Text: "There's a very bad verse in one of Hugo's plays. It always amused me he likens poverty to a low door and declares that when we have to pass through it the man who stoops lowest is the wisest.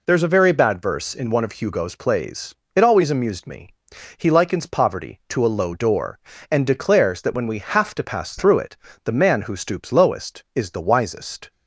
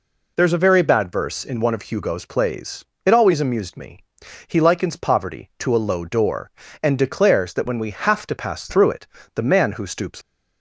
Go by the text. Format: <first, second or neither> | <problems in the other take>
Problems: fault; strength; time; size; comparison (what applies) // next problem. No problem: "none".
first | pauses between "me" and "he"; noticeable; at 3.9 s; 0.48 s long; noticeable in the first // pauses between "it" and "the"; slight; at 9.0 s; 0.26 s long; slight in the first // stops before "lowest is the wisest"; at 10.2 s